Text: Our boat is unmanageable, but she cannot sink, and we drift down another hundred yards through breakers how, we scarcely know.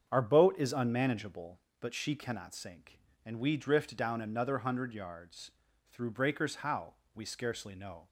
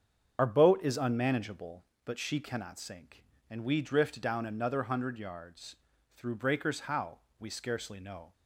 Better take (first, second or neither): first